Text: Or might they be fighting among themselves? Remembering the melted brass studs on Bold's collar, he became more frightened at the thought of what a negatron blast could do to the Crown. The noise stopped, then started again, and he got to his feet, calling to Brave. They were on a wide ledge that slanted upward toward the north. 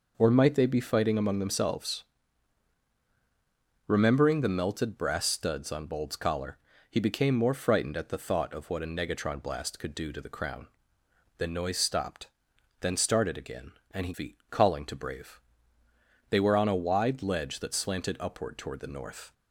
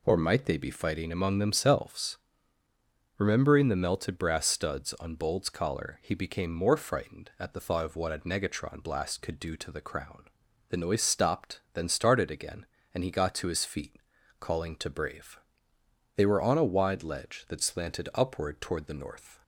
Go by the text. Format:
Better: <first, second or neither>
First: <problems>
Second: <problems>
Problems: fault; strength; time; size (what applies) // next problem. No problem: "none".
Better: second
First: skips "got to his"; at 14.1 s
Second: none